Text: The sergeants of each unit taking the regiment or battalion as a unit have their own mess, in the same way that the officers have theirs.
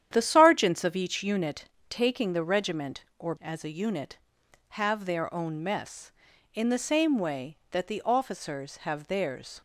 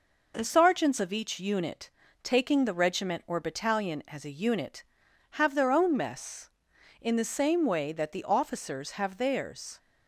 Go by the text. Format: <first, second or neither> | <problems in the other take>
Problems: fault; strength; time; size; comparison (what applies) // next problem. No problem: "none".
second | starts louder than the rest; strong; until 1.1 s; 10 dB // pauses between "unit" and "taking"; slight; at 1.6 s; 0.24 s long; slight in the second // skips "battalion"; at 3.3 s